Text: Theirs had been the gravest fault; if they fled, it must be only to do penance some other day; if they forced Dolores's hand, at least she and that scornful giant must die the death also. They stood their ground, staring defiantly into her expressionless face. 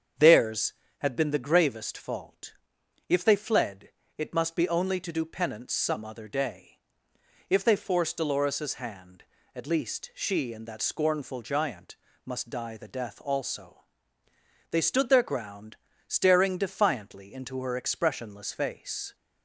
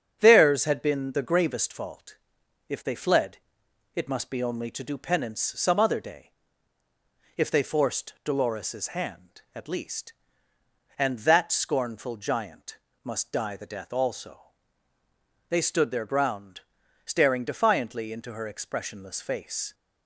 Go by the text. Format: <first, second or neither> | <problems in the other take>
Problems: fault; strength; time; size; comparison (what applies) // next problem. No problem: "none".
first | starts louder than the rest; strong; until 1.2 s; 7.5 dB; strong in the first // skips "she"; at 10.5 s // pauses between "giant" and "must"; slight; at 12.7 s; 0.26 s long; slight in the first